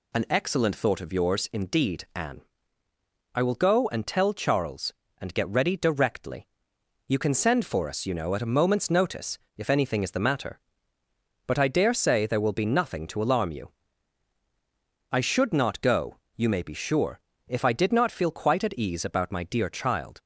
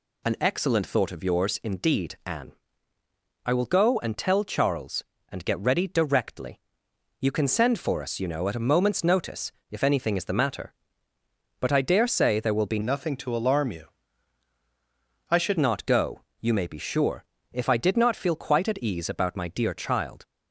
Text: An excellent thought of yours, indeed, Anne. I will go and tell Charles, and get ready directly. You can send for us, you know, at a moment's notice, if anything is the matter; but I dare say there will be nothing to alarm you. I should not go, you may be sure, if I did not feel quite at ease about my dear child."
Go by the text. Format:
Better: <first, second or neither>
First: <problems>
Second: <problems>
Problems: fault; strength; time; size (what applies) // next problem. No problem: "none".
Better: first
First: none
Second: changes voice from "nothing" to "should"; from 12.8 to 15.5 s; 2.7 s long